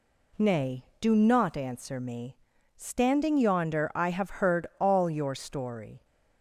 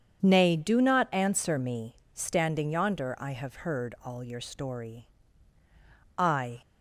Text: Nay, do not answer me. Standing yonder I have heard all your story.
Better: first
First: none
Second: starts louder than the rest; strong; until 1.2 s; 7.5 dB // goes on to say "I"; slight; from 6.1 s on; 0.46 s long

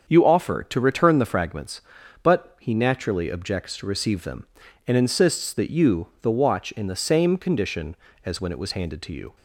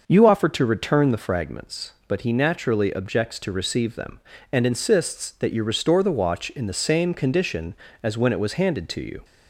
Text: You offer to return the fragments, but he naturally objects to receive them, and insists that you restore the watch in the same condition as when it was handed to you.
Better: second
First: starts louder than the rest; until 1.0 s; 7 dB // skips "restore"; at 6.1 s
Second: none

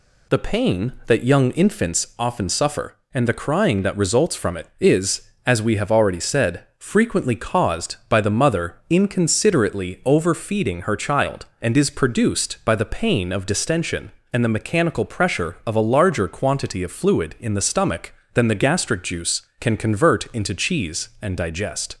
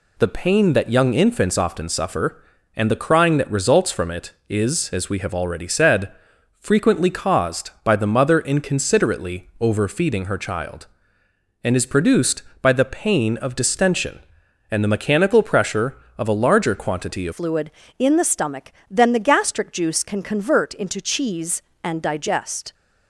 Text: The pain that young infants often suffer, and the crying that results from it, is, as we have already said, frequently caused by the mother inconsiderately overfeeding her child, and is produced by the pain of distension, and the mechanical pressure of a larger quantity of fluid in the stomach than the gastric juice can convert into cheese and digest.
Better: first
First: none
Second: changes voice at "fluid"; from 17.3 s on; 5.4 s long

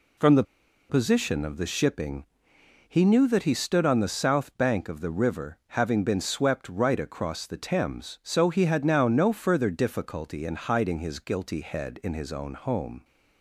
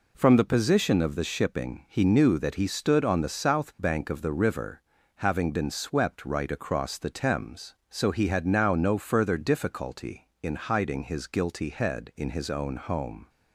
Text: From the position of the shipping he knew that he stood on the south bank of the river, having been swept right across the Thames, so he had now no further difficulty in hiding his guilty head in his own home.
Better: second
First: pauses between "the" and "position"; noticeable; at 0.4 s; 0.46 s long // pauses between "shipping" and "he"; noticeable; at 2.2 s; 0.64 s long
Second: none

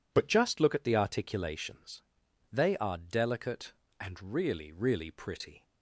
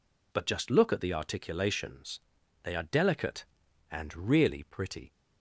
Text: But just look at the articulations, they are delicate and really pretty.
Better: second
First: says "really" twice; at 4.7 s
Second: none

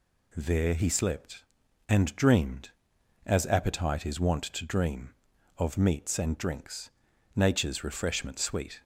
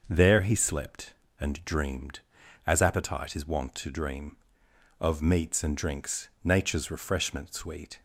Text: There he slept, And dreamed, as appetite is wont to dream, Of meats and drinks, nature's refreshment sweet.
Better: neither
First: none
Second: none

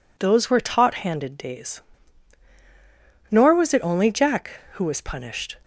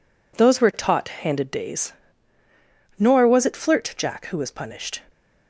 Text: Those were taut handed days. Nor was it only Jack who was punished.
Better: first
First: none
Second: says "flirt" for "only"; at 3.5 s

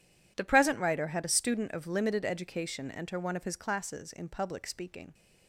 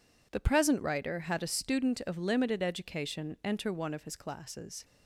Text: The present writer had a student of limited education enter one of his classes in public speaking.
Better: first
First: none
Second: stops before "in public speaking"; at 4.8 s

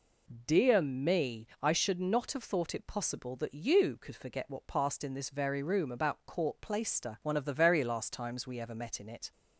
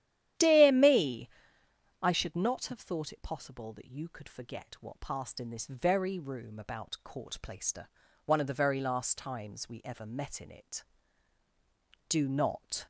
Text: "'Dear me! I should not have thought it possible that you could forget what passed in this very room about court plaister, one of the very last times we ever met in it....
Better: first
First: none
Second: starts louder than the rest; strong; until 2.1 s; 11.5 dB // goes on to say "Do not"; noticeable; from 12.0 s on; 0.76 s long

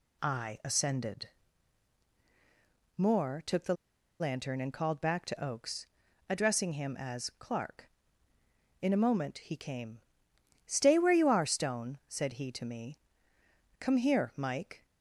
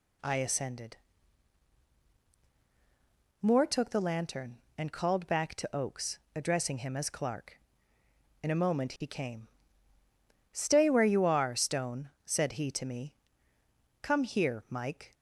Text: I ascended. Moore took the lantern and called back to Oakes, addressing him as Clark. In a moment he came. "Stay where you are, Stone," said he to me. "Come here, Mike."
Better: second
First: pauses between "the" and "lantern"; at 3.7 s; 0.45 s long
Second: none

